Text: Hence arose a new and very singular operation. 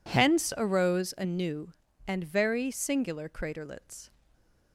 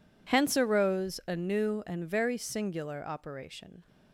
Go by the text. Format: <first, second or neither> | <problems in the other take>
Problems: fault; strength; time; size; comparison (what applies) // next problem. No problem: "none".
second | says "craterlets" for "operation"; at 3.2 s // stays silent after the last word; slight; from 4.0 s on; 0.7 s long